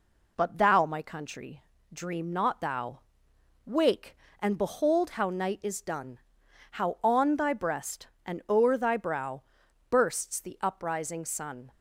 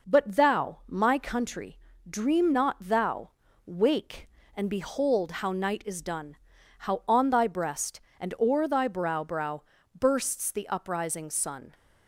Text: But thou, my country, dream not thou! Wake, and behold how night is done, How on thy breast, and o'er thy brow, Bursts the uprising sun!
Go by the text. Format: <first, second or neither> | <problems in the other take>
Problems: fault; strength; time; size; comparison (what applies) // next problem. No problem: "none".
first | says "brow" twice; at 9.2 s